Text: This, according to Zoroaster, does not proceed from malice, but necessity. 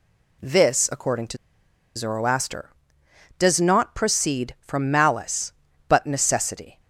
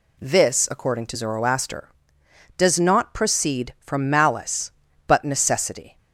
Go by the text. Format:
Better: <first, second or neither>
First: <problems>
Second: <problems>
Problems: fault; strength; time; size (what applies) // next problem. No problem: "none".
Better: second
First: pauses between "to" and "Zoroaster"; noticeable; at 1.3 s; 0.60 s long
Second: none